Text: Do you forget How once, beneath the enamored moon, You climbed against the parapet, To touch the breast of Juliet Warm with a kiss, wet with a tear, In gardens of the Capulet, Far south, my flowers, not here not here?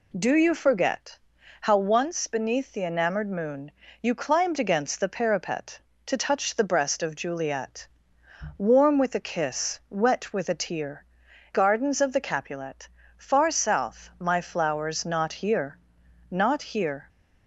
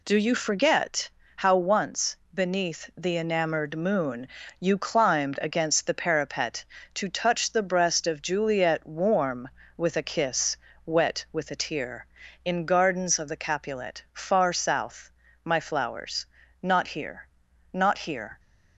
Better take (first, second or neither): second